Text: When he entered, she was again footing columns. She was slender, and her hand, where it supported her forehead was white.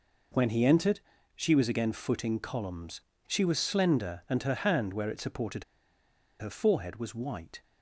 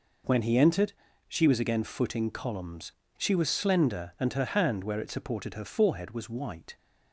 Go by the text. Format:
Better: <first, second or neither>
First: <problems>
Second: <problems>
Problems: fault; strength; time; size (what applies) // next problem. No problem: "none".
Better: second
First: pauses between "supported" and "her"; noticeable; at 5.6 s; 0.76 s long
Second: none